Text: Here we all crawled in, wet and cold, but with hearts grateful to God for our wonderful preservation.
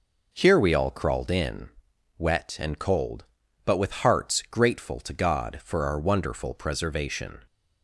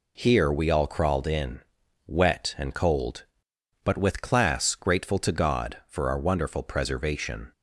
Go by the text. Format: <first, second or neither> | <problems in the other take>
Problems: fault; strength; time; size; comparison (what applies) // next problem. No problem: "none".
first | says "class" for "hearts"; at 4.2 s